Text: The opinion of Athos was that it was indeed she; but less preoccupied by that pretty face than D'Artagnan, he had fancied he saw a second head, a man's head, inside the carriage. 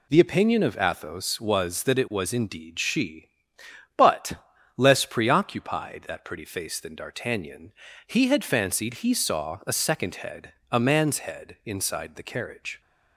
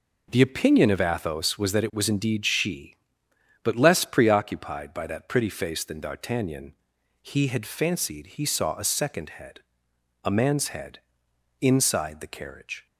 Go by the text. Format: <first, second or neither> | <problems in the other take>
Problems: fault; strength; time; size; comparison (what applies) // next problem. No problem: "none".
second | pauses between "but" and "less"; at 4.3 s; 0.42 s long // skips "by"; at 6.0 s